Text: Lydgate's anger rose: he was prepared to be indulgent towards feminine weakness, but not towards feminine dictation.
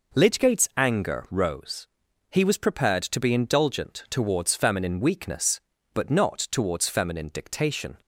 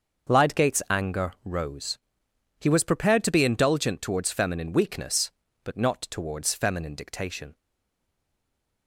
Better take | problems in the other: first | starts louder than the rest; until 1.5 s; 6.5 dB // stays silent after the last word; noticeable; from 7.5 s on; 1.3 s long

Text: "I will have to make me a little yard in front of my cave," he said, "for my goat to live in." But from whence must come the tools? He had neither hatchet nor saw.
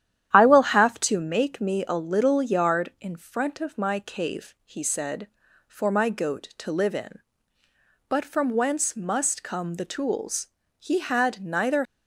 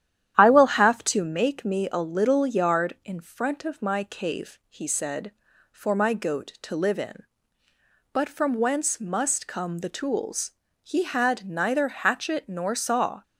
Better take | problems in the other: second | starts louder than the rest; strong; until 1.3 s; 11 dB; strong in the second // stops before "hatchet nor saw"; at 11.8 s

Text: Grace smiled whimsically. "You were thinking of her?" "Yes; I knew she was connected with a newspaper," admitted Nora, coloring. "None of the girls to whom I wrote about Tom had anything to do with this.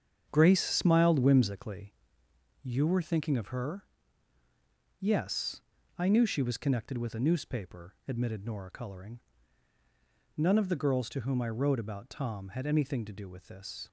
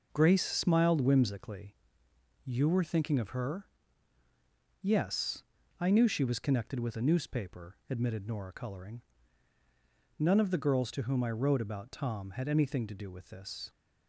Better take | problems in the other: second | starts louder than the rest; strong; until 2.1 s; 7.5 dB

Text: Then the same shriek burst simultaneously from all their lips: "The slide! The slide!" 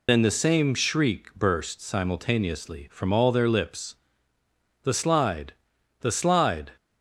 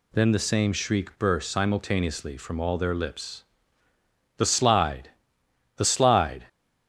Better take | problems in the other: second | loses the start of "Then"; at 0.0 s; 60 ms

